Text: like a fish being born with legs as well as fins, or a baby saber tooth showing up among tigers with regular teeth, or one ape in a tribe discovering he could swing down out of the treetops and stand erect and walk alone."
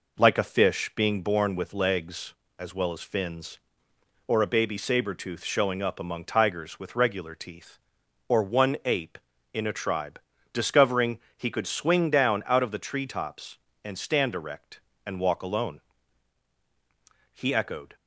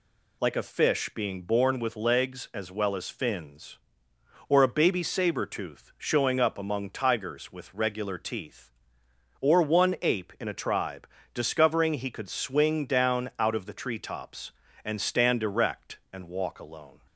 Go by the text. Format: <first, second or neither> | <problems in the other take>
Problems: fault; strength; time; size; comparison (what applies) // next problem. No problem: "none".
second | pauses between "tribe" and "discovering"; slight; at 10.1 s; 0.34 s long; slight in the second // pauses between "discovering" and "he"; slight; at 11.1 s; 0.20 s long // goes on to say "He echoed"; noticeable; from 17.3 s on; 0.62 s long